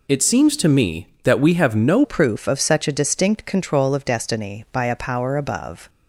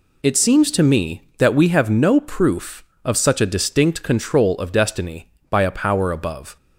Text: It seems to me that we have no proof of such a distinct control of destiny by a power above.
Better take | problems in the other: second | changes voice at "proof"; from 2.0 s on; 3.8 s long

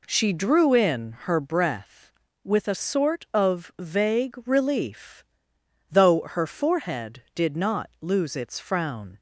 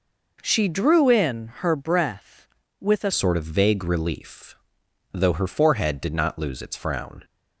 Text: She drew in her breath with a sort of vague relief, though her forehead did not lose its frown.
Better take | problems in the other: first | changes voice at "sort"; from 3.1 s on; 4.1 s long

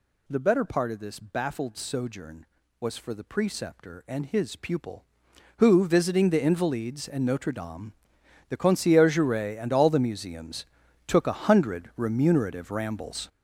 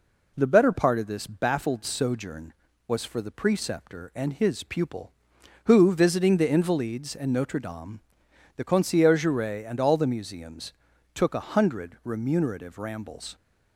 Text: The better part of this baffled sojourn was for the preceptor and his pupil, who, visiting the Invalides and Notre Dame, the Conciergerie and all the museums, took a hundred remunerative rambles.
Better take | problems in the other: second | gets louder; strong; throughout; 9 dB

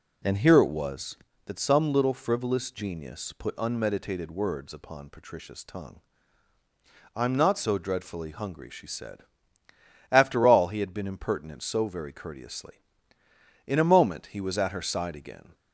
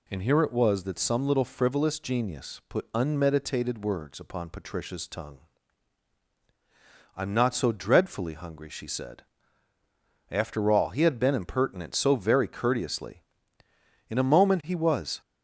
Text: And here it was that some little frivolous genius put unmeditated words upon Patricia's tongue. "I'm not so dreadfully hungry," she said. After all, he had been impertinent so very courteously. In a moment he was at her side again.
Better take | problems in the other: first | stops before "at her side again"; at 15.2 s

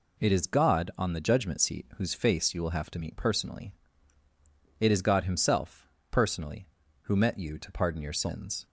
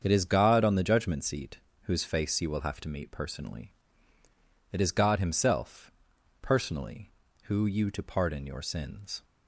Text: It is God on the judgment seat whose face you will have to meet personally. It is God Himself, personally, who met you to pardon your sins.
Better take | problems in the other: first | starts louder than the rest; strong; until 1.0 s; 7 dB // pauses between "seat" and "whose"; slight; at 1.5 s; 0.24 s long // skips "met"; at 7.6 s

